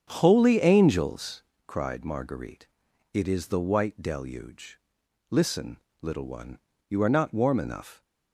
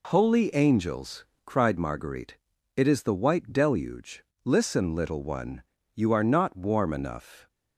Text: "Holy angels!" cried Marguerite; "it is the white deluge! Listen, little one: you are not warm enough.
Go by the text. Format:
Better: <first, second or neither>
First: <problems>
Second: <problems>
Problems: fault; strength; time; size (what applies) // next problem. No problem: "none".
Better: second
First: starts louder than the rest; strong; until 1.6 s; 8 dB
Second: none